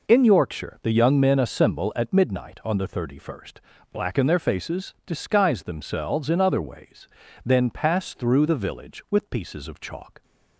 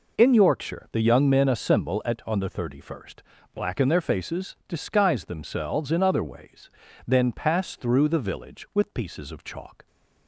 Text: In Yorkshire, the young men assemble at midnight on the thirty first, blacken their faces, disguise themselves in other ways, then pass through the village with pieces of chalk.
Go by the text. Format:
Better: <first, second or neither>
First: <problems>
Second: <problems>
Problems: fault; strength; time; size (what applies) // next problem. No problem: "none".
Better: first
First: none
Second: skips "midnight"; at 2.2 s